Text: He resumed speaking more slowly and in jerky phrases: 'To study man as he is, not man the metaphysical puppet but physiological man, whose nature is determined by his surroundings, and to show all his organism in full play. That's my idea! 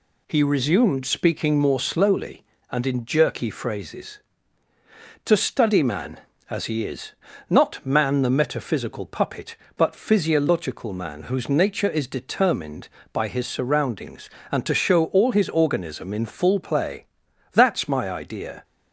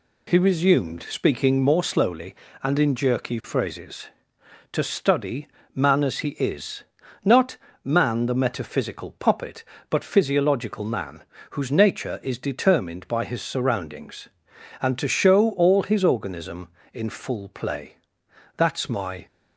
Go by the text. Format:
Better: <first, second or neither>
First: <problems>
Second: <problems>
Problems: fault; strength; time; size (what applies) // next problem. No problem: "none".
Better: first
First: none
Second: pauses between "study" and "man"; slight; at 5.4 s; 0.28 s long // pauses between "not" and "man"; slight; at 7.5 s; 0.26 s long // stops before "idea"; at 19.2 s